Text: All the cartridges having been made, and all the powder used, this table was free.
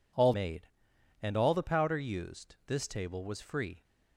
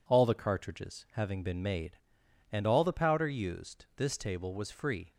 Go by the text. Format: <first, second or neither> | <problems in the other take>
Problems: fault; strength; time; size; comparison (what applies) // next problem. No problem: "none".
second | skips "the cartridges having been"; at 0.3 s